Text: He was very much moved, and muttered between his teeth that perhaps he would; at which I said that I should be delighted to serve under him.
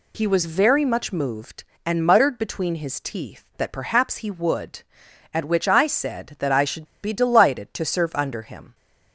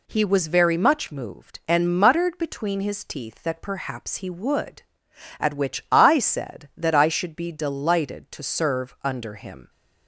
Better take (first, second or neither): second